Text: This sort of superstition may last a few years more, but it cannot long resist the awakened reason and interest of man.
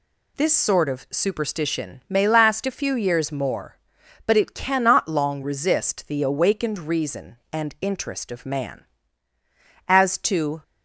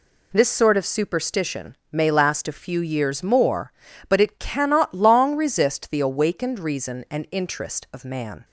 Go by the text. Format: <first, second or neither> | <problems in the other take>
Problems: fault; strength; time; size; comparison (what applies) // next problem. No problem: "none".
second | goes on to say "As to"; noticeable; from 9.8 s on; 0.76 s long